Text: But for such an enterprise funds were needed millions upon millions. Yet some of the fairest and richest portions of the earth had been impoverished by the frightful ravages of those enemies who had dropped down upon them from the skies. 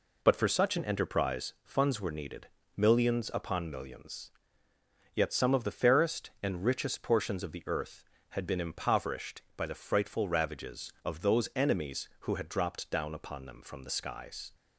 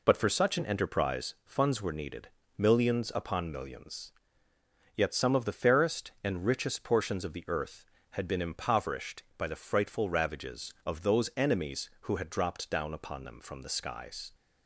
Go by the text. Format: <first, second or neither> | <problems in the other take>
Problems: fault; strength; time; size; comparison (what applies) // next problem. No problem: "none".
neither | pauses between "needed" and "millions"; slight; the same in both